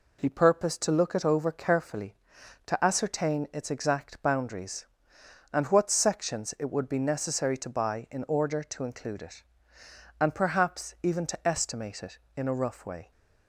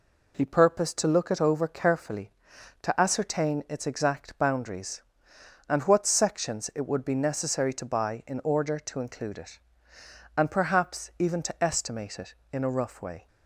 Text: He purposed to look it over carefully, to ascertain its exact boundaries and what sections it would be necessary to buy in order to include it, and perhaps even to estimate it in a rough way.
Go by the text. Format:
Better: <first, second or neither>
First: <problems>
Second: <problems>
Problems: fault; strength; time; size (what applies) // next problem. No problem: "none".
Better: neither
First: none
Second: none